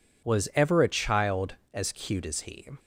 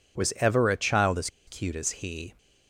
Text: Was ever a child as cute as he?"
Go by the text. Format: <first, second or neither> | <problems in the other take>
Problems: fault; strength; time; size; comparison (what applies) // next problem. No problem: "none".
first | pauses between "as" and "cute"; slight; at 1.2 s; 0.18 s long